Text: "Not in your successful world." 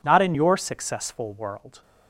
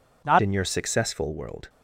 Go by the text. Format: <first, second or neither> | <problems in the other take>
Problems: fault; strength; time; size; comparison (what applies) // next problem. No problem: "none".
first | changes voice at "in"; from 0.4 s on; 1.2 s long